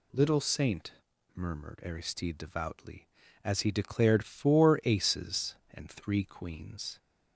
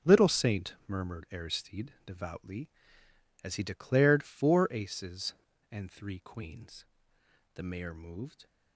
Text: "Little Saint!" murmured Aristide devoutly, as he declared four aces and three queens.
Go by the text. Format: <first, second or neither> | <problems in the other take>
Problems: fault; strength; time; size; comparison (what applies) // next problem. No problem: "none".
first | starts louder than the rest; until 1.1 s; 6.5 dB // goes on to say "The Mayor moved"; noticeable; from 7.5 s on; 0.92 s long